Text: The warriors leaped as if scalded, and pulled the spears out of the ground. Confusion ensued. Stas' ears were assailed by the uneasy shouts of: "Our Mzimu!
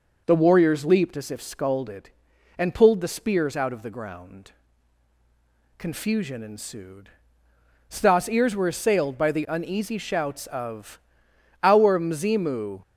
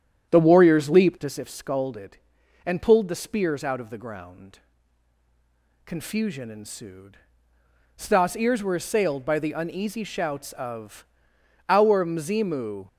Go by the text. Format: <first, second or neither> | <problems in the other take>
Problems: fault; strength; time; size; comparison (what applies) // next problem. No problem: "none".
first | starts louder than the rest; strong; until 1.4 s; 9.5 dB